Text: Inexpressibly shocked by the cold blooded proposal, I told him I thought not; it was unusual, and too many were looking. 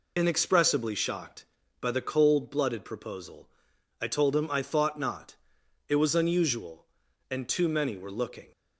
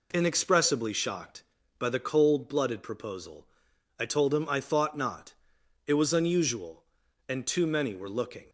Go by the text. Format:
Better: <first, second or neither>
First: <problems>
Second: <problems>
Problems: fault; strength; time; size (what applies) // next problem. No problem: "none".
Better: second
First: loses the start of "Inexpressibly"; at 0.1 s; 45 ms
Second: none